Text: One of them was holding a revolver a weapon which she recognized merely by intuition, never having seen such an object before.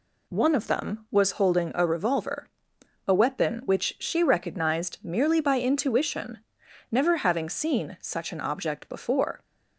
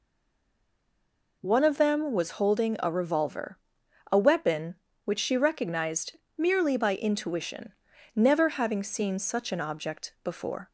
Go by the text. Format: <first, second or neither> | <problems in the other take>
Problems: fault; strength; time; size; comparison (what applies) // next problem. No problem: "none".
first | stays silent before the first word; noticeable; until 1.4 s; 1.4 s long // pauses between "revolver" and "a"; noticeable; at 3.5 s; 0.56 s long; noticeable in the first // pauses between "recognized" and "merely"; slight; at 6.1 s; 0.18 s long